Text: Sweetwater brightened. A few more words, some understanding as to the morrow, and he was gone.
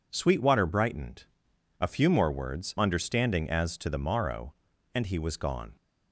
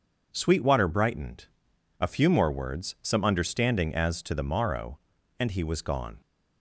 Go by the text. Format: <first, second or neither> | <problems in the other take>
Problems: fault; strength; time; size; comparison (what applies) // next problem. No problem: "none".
second | skips "some"; at 2.7 s